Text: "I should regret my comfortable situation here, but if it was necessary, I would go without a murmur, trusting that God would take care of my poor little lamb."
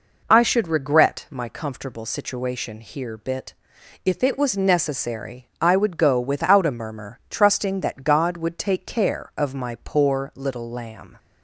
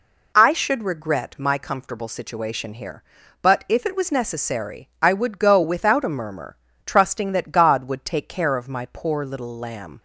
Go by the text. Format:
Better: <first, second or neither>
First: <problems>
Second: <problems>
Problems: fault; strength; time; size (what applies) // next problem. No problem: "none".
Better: second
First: says "bit" for "but"; at 3.1 s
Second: none